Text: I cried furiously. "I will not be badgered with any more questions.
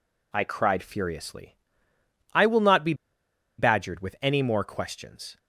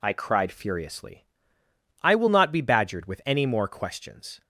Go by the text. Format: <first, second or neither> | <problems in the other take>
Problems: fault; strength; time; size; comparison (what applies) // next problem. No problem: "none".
second | pauses between "be" and "badgered"; noticeable; at 2.9 s; 0.64 s long